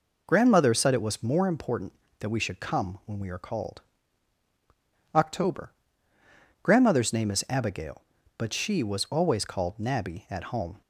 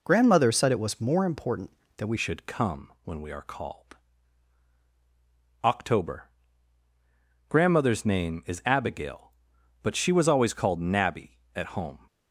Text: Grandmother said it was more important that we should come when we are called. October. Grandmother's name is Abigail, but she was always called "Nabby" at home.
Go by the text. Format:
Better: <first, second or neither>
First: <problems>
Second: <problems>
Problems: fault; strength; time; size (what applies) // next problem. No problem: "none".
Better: first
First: none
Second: changes voice at "should"; from 2.1 s on; 9.9 s long